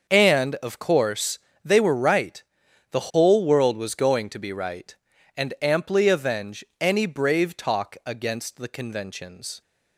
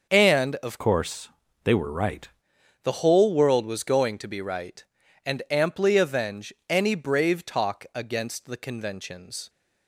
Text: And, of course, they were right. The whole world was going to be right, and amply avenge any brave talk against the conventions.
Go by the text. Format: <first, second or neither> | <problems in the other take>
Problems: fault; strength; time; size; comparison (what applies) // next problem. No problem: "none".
first | starts louder than the rest; until 1.1 s; 6 dB; also in the first // changes voice from "course" to "right"; from 0.7 to 2.2 s; 1.5 s long // pauses between "avenge" and "any"; slight; at 6.5 s; 0.16 s long; slight in the first